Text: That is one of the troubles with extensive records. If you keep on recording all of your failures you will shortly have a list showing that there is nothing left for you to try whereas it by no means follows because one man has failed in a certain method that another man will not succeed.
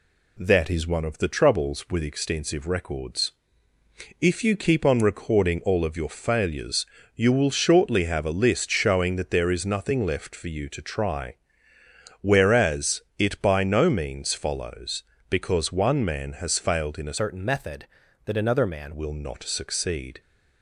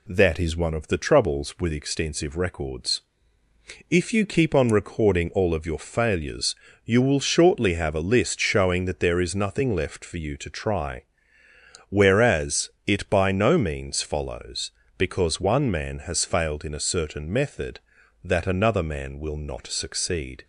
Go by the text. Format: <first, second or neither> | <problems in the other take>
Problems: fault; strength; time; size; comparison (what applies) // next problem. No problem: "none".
second | pauses between "failures" and "you"; slight; at 6.8 s; 0.30 s long; slight in the second // pauses between "try" and "whereas"; noticeable; at 11.3 s; 0.88 s long; noticeable in the second // pauses between "whereas" and "it"; slight; at 13.0 s; 0.16 s long; slight in the second // changes voice from "certain" to "man"; from 17.1 to 18.9 s; 1.8 s long